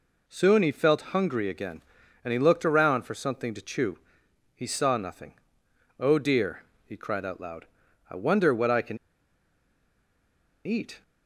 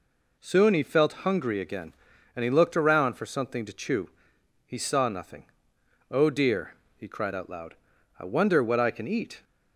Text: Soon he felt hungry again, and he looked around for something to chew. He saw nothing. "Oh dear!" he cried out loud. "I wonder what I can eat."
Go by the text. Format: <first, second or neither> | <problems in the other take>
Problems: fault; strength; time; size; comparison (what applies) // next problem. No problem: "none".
second | pauses between "can" and "eat"; strong; at 8.9 s; 1.6 s long